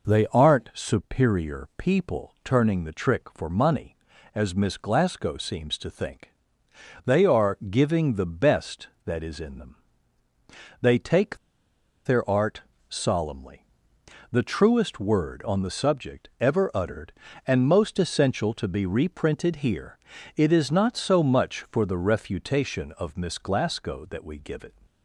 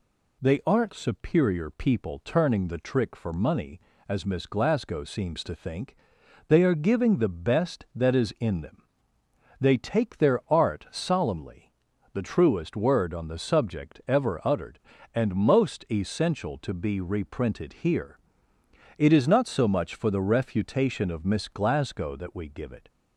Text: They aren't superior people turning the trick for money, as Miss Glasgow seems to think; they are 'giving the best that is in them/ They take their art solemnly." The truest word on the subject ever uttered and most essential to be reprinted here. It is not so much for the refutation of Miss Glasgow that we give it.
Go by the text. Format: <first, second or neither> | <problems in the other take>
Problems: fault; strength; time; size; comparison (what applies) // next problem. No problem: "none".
second | pauses between "take" and "their"; noticeable; at 11.3 s; 0.68 s long // pauses between "art" and "solemnly"; slight; at 12.6 s; 0.28 s long